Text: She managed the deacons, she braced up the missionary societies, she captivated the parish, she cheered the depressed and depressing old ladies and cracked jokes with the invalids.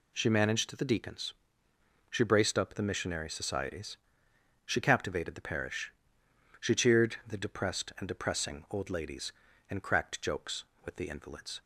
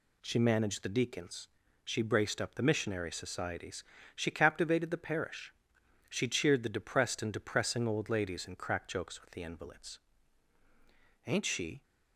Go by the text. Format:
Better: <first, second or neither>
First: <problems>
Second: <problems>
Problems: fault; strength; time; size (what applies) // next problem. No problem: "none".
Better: first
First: none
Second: goes on to say "Ain't she"; from 11.2 s on; 0.56 s long